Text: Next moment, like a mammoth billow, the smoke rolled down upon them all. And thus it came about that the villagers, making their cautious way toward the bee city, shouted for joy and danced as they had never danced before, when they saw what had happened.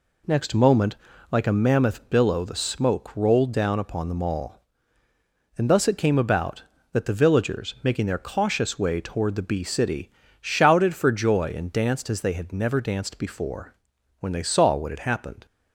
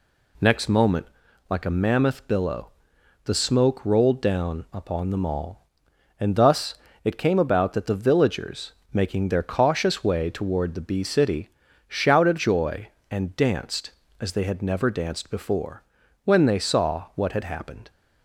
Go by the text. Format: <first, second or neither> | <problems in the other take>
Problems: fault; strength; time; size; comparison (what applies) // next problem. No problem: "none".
first | pauses between "thus" and "it"; slight; at 6.7 s; 0.30 s long // skips "for"; at 12.3 s